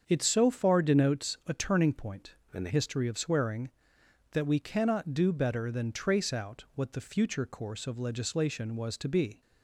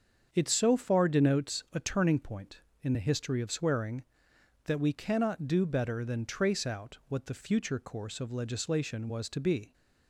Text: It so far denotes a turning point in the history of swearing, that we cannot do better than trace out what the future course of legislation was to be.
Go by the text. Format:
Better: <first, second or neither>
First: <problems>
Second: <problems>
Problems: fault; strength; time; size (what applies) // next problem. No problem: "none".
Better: second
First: starts louder than the rest; strong; until 1.0 s; 7 dB // changes voice from "in" to "the"; from 2.5 to 2.6 s; 0.1 s long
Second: starts louder than the rest; until 1.3 s; 7 dB